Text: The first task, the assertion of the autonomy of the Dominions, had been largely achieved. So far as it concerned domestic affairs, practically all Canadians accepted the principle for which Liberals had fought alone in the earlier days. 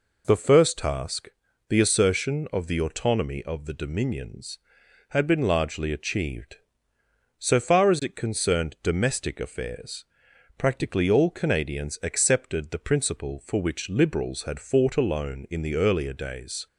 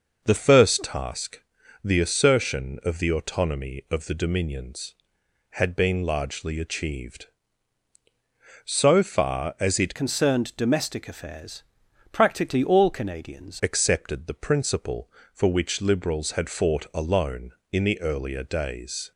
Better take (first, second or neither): first